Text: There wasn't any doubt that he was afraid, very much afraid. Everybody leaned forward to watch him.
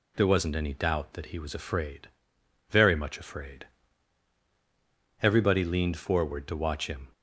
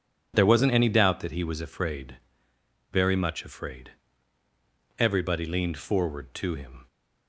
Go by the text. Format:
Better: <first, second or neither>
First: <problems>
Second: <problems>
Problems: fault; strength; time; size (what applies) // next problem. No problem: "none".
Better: first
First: none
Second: skips "watch"; at 6.5 s